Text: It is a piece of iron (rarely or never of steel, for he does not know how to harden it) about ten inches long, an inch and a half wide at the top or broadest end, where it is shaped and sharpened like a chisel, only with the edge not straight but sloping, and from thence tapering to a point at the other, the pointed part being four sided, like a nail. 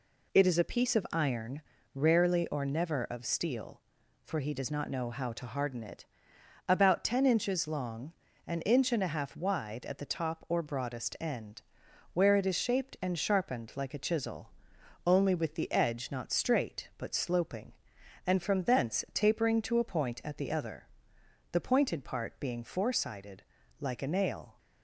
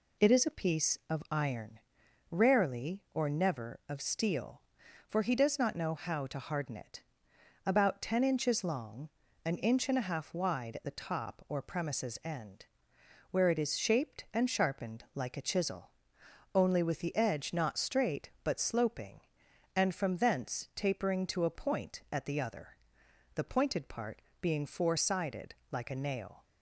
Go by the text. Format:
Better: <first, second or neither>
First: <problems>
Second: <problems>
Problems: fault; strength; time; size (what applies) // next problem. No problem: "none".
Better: first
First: none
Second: says "premises" for "broadest"; at 11.6 s // pauses between "part" and "being"; slight; at 24.1 s; 0.22 s long